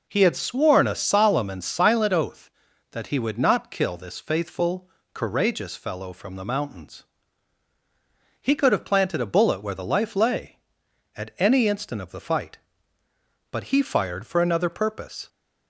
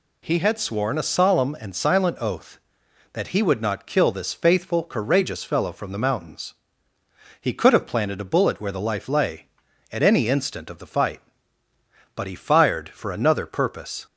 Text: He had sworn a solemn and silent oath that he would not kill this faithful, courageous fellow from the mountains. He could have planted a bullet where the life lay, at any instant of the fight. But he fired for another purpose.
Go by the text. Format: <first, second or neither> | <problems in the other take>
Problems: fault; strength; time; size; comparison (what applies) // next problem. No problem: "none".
neither | none